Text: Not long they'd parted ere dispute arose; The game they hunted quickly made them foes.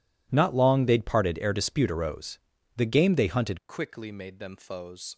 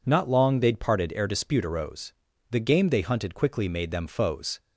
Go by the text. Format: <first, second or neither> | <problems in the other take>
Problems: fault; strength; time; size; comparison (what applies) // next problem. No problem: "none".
second | changes voice at "quickly"; from 3.6 s on; 1.5 s long